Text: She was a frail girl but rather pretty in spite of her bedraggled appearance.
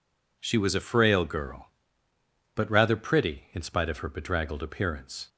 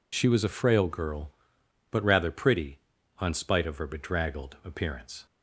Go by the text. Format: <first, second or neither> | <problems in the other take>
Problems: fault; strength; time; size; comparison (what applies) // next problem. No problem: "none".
first | says "on" for "in"; at 3.1 s